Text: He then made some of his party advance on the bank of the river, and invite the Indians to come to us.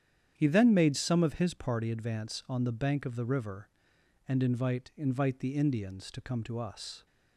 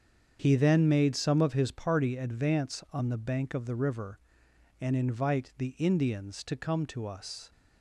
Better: second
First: starts louder than the rest; strong; until 1.3 s; 9 dB // says "invite" twice; at 4.9 s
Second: starts louder than the rest; strong; until 1.4 s; 7 dB

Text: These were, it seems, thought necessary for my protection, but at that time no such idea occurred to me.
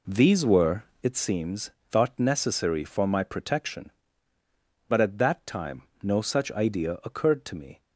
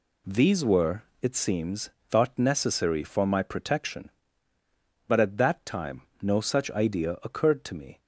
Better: second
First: starts louder than the rest; slight; until 1.2 s; 3 dB // pauses between "time" and "no"; slight; at 5.8 s; 0.18 s long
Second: pauses between "time" and "no"; slight; at 6.0 s; 0.18 s long

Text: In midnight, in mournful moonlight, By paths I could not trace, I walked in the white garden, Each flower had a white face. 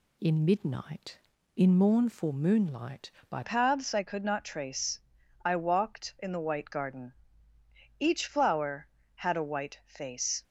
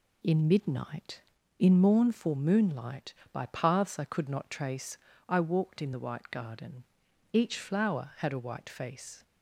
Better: second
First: changes voice at "paths"; from 3.4 s on; 7.0 s long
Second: none

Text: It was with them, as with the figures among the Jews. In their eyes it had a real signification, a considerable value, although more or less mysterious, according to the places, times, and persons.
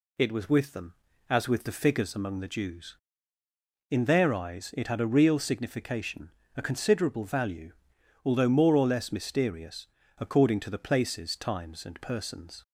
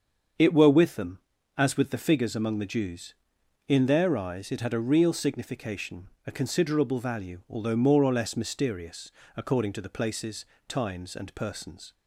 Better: first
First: none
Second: starts louder than the rest; until 1.7 s; 7 dB // says "were" for "was"; at 0.5 s

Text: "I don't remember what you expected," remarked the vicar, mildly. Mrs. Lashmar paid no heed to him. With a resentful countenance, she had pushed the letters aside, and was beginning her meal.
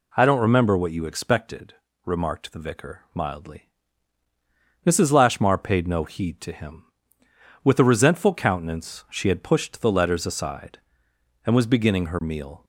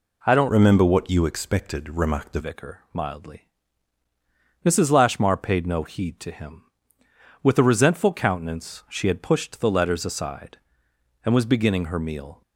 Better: first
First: none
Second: changes voice from "remember" to "the"; from 0.4 to 2.3 s; 1.9 s long

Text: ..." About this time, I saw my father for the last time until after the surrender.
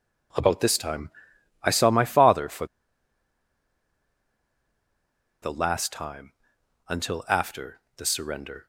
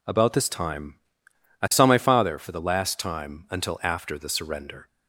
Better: second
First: pauses between "for" and "the"; strong; at 2.6 s; 2.7 s long // pauses between "time" and "until"; noticeable; at 6.3 s; 0.56 s long // pauses between "after" and "the"; slight; at 7.7 s; 0.18 s long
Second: none

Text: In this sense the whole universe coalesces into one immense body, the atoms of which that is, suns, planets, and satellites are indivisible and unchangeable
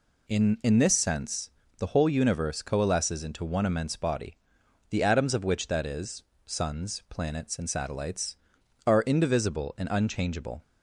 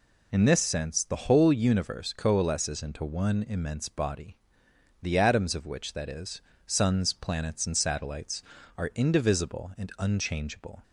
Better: second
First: says "In" twice; at 0.6 s // pauses between "sense" and "the"; slight; at 1.5 s; 0.26 s long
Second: none

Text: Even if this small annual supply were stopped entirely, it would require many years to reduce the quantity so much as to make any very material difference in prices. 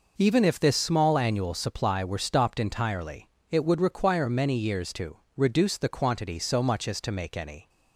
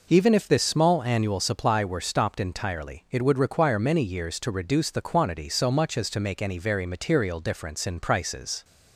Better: second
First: pauses between "to" and "reduce"; slight; at 5.1 s; 0.20 s long // stops before "very material difference in prices"; at 7.6 s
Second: none

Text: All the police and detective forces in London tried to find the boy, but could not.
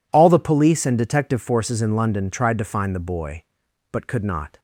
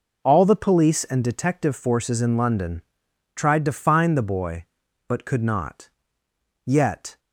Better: first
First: none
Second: pauses between "London" and "tried"; noticeable; at 2.8 s; 0.52 s long // goes on to say "Yet"; from 6.6 s on; 0.54 s long

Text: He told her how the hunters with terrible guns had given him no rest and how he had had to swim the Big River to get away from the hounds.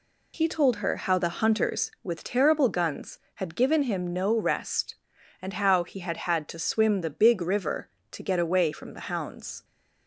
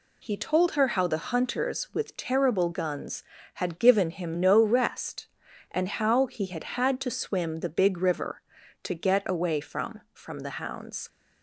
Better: first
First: none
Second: says "from" twice; at 10.1 s

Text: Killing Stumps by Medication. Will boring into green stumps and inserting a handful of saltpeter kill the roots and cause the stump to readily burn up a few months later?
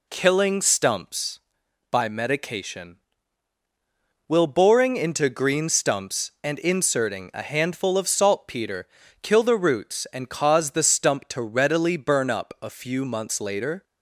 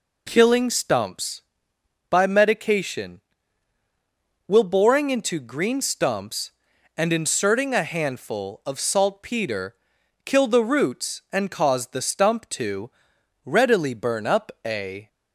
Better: first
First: pauses between "saltpeter" and "kill"; slight; at 8.8 s; 0.34 s long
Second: pauses between "saltpeter" and "kill"; noticeable; at 9.7 s; 0.52 s long // pauses between "to" and "readily"; noticeable; at 12.8 s; 0.56 s long // stops before "few months later"; at 15.0 s

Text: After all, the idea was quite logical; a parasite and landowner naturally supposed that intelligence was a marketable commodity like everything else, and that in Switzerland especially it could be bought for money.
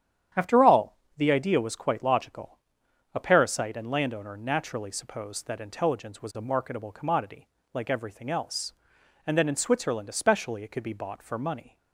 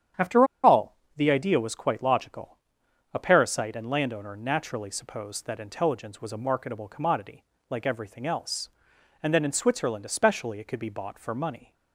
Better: first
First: starts louder than the rest; strong; until 1.5 s; 9.5 dB // pauses between "commodity" and "like"; slight; at 7.4 s; 0.26 s long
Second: starts louder than the rest; strong; until 1.5 s; 9.5 dB // pauses between "After" and "all"; slight; at 0.4 s; 0.17 s long // pauses between "commodity" and "like"; slight; at 7.4 s; 0.26 s long

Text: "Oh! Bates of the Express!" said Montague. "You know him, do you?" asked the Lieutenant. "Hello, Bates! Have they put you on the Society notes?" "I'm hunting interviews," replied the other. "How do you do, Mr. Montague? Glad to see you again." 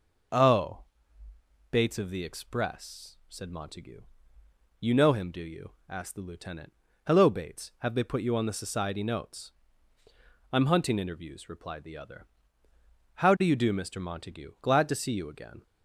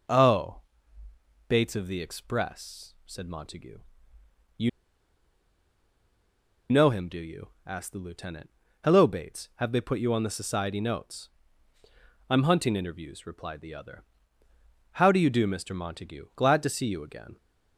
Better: first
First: starts louder than the rest; noticeable; until 2.2 s; 6 dB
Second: starts louder than the rest; noticeable; until 1.9 s; 6 dB // pauses between "You" and "know"; strong; at 4.6 s; 2.0 s long

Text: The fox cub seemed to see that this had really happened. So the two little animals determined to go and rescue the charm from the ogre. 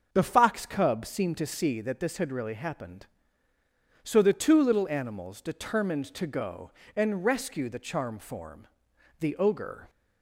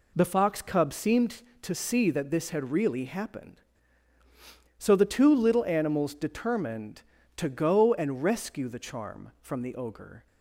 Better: second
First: starts louder than the rest; until 1.1 s; 6.5 dB // says "form" for "from"; at 8.1 s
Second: none

